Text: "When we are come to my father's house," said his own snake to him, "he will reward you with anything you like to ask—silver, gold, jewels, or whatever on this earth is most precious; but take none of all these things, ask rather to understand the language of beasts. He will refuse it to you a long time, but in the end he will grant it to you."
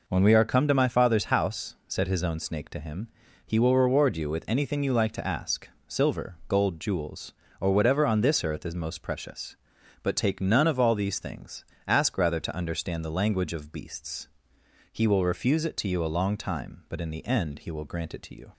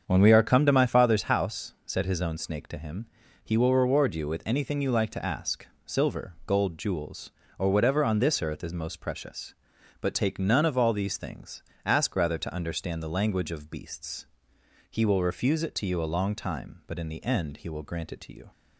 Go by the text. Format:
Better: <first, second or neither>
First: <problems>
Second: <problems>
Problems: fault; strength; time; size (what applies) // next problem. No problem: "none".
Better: first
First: none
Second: starts louder than the rest; strong; until 1.3 s; 7 dB